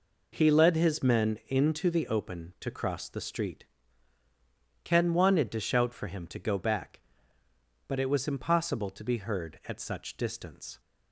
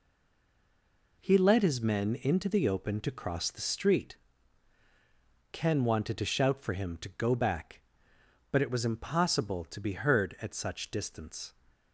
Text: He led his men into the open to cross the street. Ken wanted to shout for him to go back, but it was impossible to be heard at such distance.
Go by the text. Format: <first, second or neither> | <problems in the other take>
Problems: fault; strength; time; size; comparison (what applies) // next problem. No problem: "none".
first | stays silent before the first word; noticeable; until 1.1 s; 1.1 s long